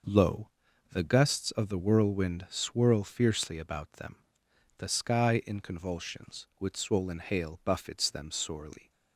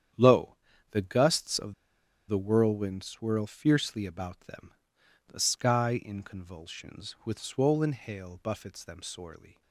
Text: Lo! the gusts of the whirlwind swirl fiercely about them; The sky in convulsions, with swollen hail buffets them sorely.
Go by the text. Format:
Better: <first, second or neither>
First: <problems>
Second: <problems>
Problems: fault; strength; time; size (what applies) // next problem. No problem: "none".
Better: first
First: none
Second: starts louder than the rest; strong; until 1.5 s; 9 dB // pauses between "of" and "the"; noticeable; at 1.7 s; 0.54 s long